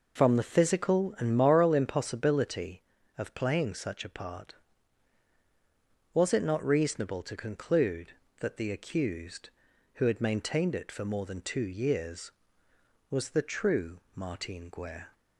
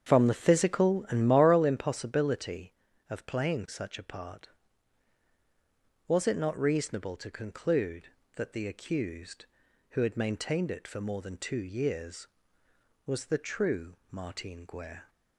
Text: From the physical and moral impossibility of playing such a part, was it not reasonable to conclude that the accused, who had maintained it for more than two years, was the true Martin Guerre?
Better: first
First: none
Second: starts louder than the rest; strong; until 1.7 s; 8 dB

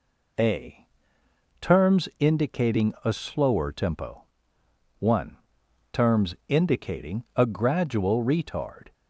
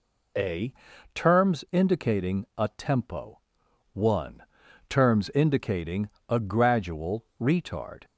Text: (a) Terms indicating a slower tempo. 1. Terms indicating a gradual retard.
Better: first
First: none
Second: skips "slower"; at 2.6 s // pauses between "indicating" and "a"; slight; at 6.0 s; 0.18 s long // pauses between "gradual" and "retard"; slight; at 7.2 s; 0.16 s long

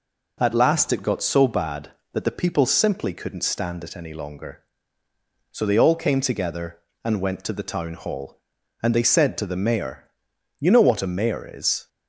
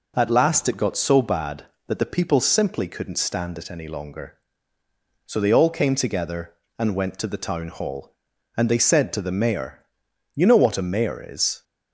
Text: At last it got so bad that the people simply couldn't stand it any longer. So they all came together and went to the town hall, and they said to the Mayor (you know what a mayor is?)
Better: neither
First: none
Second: none

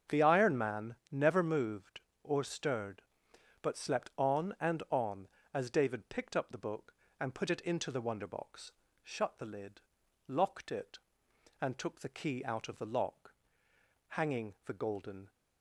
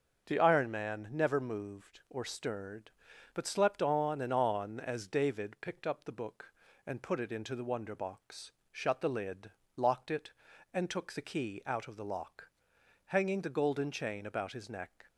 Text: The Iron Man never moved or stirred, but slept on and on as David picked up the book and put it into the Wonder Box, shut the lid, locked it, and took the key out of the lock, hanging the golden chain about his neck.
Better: second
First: starts louder than the rest; strong; until 1.2 s; 7 dB // pauses between "Man" and "never"; slight; at 0.9 s; 0.16 s long // stops before "chain about his neck"; at 15.2 s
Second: starts louder than the rest; until 1.2 s; 6.5 dB

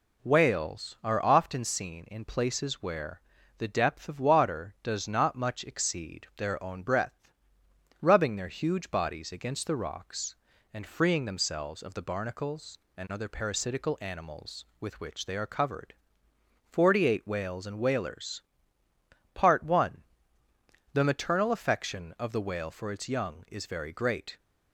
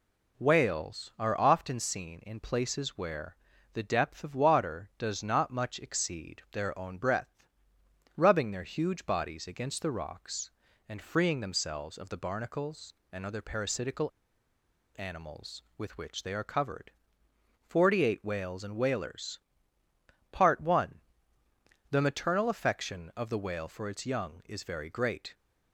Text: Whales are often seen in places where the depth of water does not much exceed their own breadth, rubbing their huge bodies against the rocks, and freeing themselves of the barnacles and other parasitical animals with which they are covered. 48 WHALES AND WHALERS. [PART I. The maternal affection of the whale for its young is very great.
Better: first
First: pauses between "where" and "the"; slight; at 3.2 s; 0.36 s long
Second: pauses between "where" and "the"; slight; at 3.3 s; 0.36 s long // pauses between "parasitical" and "animals"; noticeable; at 14.1 s; 0.86 s long

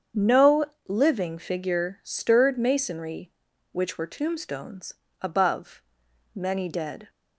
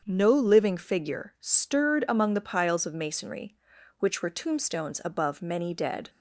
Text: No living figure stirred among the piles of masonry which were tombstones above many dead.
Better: second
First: starts louder than the rest; strong; until 1.4 s; 7.5 dB // pauses between "No" and "living"; slight; at 0.6 s; 0.24 s long // skips "among the piles of"; at 2.5 s // pauses between "tombstones" and "above"; slight; at 4.9 s; 0.28 s long // pauses between "above" and "many"; noticeable; at 5.8 s; 0.52 s long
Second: starts louder than the rest; until 1.0 s; 7 dB

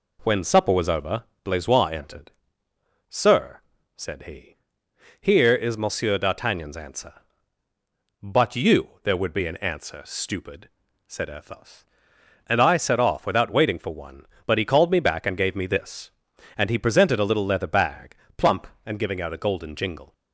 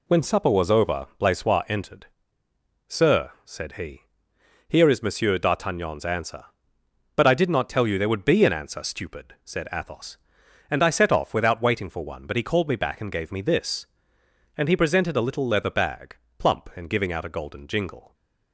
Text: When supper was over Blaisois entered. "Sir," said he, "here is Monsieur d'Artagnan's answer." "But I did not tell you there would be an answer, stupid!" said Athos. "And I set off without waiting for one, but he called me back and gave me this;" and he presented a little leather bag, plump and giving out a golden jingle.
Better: second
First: pauses between "over" and "Blaisois"; slight; at 1.2 s; 0.20 s long // skips "I did not tell"; at 8.5 s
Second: none

